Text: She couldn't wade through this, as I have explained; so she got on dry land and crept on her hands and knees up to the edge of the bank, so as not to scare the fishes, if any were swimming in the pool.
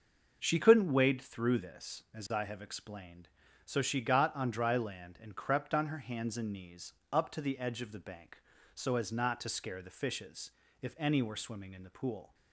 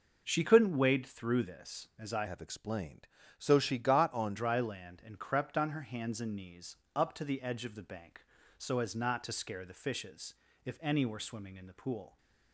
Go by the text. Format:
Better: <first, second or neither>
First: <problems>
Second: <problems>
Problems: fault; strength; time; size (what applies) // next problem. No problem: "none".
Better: first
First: pauses between "knees" and "up"; slight; at 6.9 s; 0.22 s long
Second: changes voice from "have" to "on"; from 2.2 to 4.3 s; 2.1 s long // pauses between "knees" and "up"; slight; at 6.7 s; 0.22 s long